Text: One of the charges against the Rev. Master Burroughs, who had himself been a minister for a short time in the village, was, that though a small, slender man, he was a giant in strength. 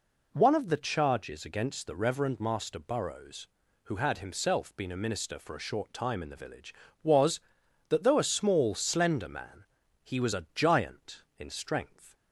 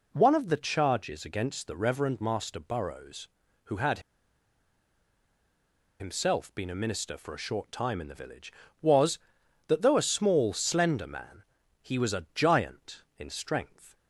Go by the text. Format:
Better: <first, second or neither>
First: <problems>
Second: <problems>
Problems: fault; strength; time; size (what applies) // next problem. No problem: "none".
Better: first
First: none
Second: pauses between "had" and "himself"; strong; at 3.9 s; 1.9 s long